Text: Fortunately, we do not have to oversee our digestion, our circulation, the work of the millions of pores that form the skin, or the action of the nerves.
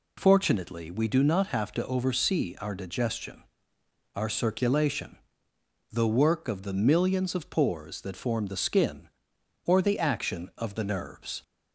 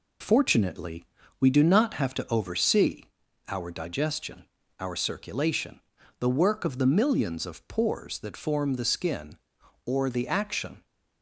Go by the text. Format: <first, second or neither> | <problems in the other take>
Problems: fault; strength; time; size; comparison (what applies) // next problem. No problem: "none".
first | pauses between "oversee" and "our"; at 3.0 s; 0.42 s long // stops before "of the nerves"; at 10.8 s